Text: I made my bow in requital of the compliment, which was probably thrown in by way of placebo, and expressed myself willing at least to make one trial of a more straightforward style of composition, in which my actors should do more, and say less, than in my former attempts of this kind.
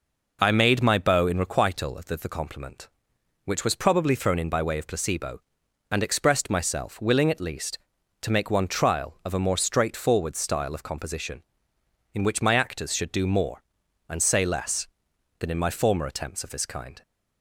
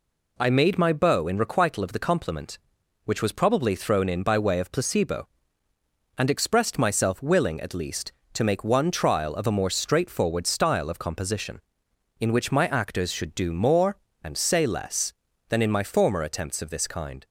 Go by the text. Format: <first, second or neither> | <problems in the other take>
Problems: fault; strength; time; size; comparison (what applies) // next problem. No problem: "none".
second | says "the" twice; at 2.1 s